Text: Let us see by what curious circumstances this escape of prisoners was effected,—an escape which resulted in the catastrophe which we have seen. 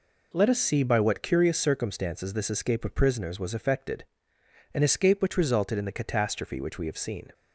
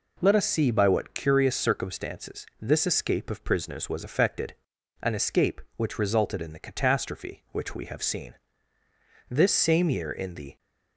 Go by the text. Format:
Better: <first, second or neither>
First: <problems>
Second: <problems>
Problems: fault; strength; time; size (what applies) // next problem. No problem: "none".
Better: first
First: none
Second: pauses between "circumstances" and "this"; slight; at 2.4 s; 0.16 s long // goes on to say "This same year in the"; noticeable; from 9.2 s on; 1.2 s long